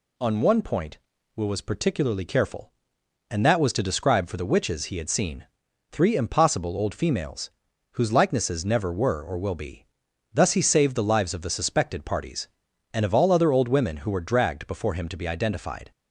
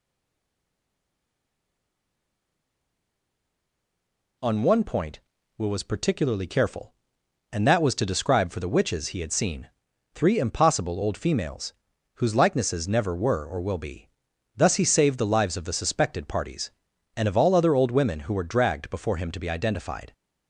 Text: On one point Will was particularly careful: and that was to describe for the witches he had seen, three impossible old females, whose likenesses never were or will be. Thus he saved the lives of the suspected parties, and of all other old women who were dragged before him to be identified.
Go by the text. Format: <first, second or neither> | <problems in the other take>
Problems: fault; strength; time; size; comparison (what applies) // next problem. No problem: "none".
first | stays silent before the first word; strong; until 4.3 s; 4.3 s long